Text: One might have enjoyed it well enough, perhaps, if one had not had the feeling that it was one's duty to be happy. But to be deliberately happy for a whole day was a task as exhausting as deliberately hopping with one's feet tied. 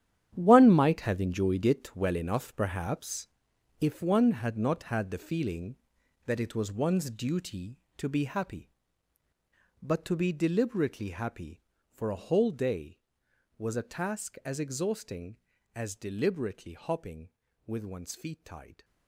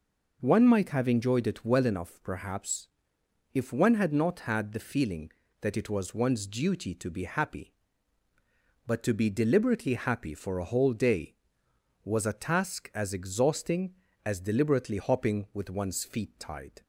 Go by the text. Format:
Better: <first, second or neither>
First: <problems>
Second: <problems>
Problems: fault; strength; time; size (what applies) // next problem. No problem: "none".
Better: second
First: gets quieter; strong; throughout; 12.5 dB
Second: none